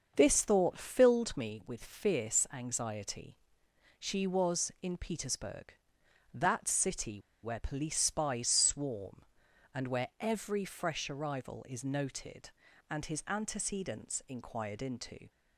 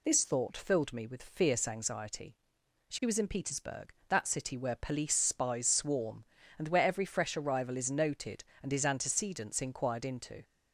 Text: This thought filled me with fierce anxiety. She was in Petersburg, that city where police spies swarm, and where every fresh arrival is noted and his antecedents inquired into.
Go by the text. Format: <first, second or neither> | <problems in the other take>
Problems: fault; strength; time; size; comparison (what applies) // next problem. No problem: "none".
second | starts louder than the rest; until 1.1 s; 6.5 dB // pauses between "city" and "where"; slight; at 7.2 s; 0.22 s long